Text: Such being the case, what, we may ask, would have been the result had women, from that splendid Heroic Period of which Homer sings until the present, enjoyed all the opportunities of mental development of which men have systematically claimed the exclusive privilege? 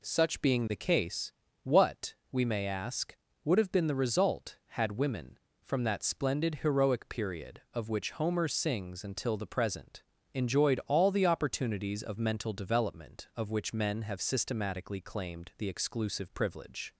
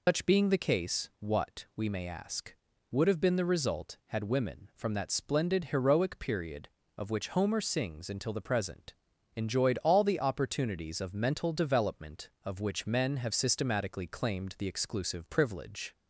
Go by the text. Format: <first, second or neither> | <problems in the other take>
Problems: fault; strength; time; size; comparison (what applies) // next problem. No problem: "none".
first | loses the start of "Such"; at 0.0 s; 145 ms